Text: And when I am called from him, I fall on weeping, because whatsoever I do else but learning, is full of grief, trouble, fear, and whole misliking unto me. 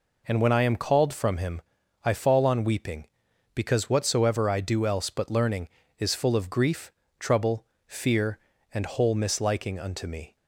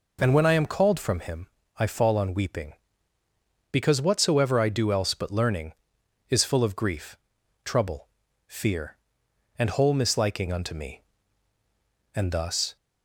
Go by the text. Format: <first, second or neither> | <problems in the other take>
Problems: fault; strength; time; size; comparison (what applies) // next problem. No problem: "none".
first | goes on to say "And thus"; noticeable; from 12.1 s on; 0.62 s long